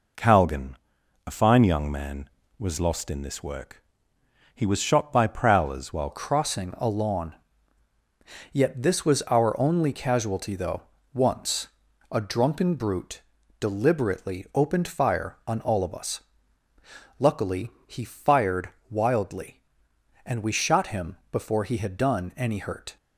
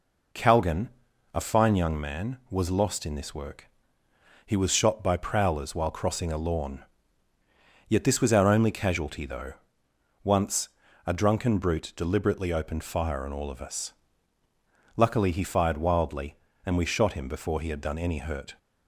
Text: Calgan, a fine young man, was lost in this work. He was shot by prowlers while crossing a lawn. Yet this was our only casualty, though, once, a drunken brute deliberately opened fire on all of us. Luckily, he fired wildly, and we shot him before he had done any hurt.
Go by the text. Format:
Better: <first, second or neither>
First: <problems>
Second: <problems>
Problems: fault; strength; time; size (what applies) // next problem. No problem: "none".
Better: second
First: changes voice at "crossing"; from 6.1 s on; 16.8 s long // pauses between "brute" and "deliberately"; at 13.2 s; 0.38 s long // pauses between "fired" and "wildly"; slight; at 18.6 s; 0.22 s long // pauses between "him" and "before"; slight; at 21.1 s; 0.16 s long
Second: none